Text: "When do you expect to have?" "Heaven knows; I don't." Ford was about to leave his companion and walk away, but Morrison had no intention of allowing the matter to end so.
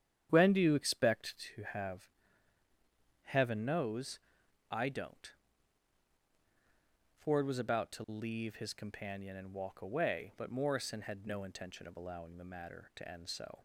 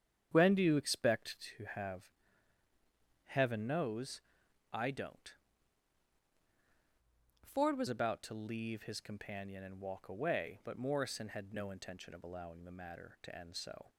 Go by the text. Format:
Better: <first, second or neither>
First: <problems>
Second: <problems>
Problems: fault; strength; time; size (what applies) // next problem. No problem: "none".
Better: first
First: starts louder than the rest; strong; until 1.3 s; 9.5 dB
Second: starts louder than the rest; strong; until 1.3 s; 8.5 dB // changes voice from "Ford" to "was"; from 7.4 to 7.8 s; 0.4 s long